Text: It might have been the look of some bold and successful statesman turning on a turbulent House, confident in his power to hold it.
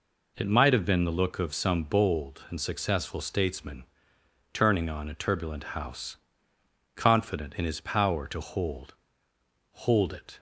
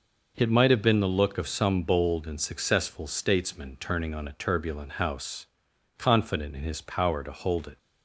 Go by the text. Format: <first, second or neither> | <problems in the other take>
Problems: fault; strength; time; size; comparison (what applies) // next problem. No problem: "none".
second | pauses between "statesman" and "turning"; noticeable; at 3.8 s; 0.68 s long // says "hold" twice; at 9.7 s